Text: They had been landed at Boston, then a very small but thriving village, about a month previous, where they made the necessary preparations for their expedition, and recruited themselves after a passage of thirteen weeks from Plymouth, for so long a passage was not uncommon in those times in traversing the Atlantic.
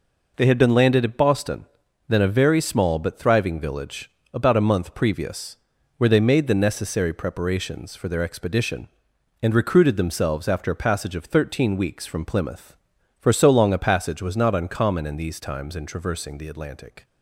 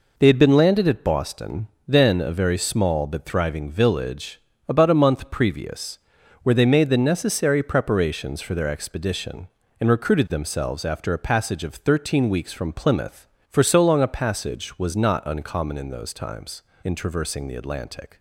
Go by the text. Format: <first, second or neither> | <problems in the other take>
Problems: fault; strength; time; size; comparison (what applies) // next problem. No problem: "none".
second | says "these" for "those"; at 15.1 s